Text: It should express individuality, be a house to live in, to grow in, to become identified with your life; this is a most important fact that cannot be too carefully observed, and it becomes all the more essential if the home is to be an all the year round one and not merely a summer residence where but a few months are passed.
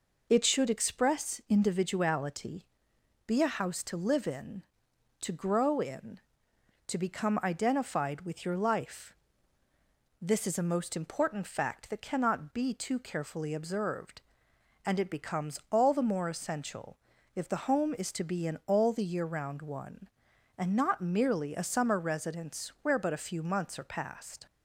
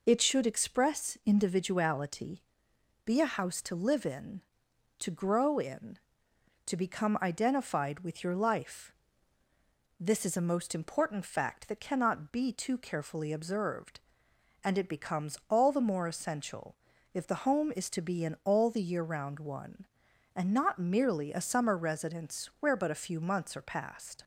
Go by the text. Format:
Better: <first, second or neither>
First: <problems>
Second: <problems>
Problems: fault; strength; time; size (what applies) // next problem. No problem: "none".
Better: neither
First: pauses between "essential" and "if"; slight; at 16.9 s; 0.36 s long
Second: pauses between "essential" and "if"; slight; at 16.7 s; 0.36 s long